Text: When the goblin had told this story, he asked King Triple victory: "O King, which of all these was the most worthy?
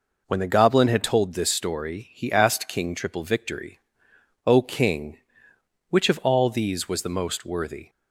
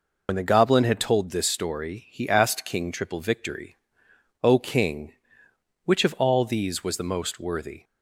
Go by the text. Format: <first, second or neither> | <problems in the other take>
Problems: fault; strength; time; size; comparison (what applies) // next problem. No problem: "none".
first | loses the start of "When"; at 0.2 s; 70 ms